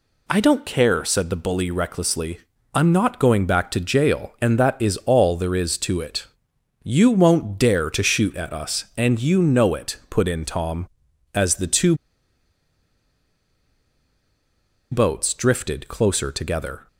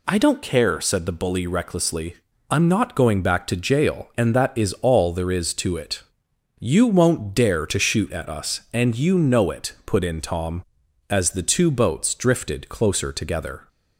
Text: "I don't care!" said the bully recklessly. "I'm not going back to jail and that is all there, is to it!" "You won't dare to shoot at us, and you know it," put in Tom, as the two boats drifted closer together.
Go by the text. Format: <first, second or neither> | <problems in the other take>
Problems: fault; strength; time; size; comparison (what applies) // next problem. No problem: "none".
second | pauses between "two" and "boats"; strong; at 11.9 s; 2.9 s long